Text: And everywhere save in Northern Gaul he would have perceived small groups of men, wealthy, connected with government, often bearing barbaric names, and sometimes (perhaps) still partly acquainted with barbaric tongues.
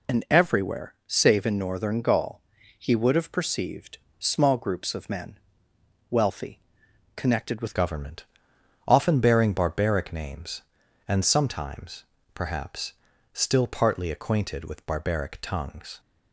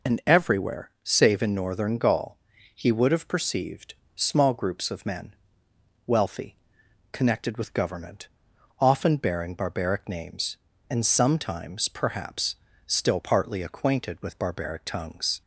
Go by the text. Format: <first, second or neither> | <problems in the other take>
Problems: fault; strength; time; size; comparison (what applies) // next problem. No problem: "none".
second | pauses between "Gaul" and "he"; at 2.4 s; 0.38 s long; also in the second // pauses between "perceived" and "small"; slight; at 3.9 s; 0.22 s long; slight in the second // changes voice at "government"; from 7.7 s on; 8.2 s long